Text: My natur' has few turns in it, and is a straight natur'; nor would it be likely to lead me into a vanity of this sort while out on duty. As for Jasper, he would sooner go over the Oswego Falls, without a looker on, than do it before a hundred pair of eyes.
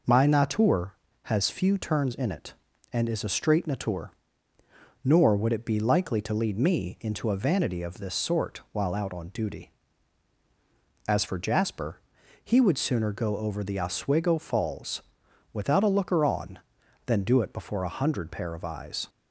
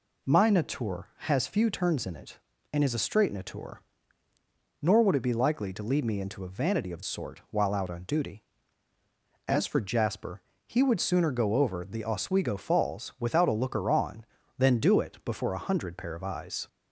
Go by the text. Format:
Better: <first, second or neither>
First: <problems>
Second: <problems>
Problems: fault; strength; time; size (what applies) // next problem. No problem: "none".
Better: first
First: none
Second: skips "this"; at 7.0 s